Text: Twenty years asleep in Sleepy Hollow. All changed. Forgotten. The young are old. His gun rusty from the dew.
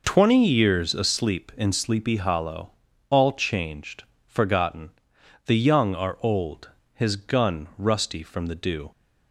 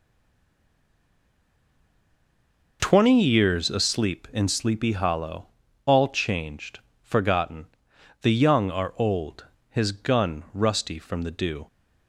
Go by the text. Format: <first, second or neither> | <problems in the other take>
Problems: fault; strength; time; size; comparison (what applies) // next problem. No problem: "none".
first | stays silent before the first word; strong; until 2.7 s; 2.7 s long